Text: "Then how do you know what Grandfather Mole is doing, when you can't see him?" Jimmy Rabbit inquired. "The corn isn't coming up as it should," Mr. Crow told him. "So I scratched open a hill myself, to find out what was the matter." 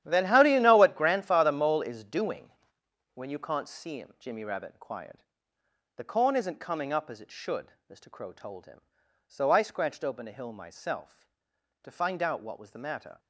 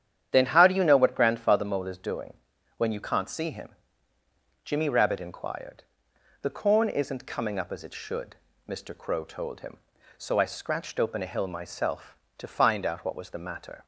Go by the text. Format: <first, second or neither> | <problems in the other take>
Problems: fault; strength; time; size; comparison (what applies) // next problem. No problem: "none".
second | gets quieter; strong; throughout; 13.5 dB // starts louder than the rest; strong; until 1.0 s; 11.5 dB; strong in the second